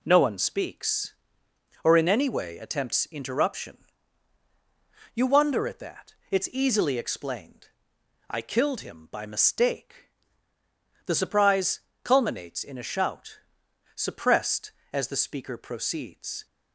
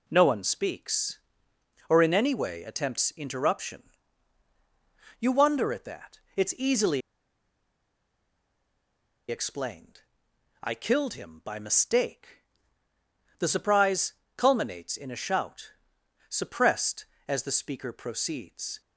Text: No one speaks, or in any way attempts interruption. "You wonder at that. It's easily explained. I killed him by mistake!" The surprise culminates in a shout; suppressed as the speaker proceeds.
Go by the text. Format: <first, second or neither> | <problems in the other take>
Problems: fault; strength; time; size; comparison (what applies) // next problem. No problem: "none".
first | pauses between "easily" and "explained"; strong; at 7.0 s; 2.2 s long // pauses between "surprise" and "culminates"; slight; at 14.1 s; 0.20 s long; slight in the first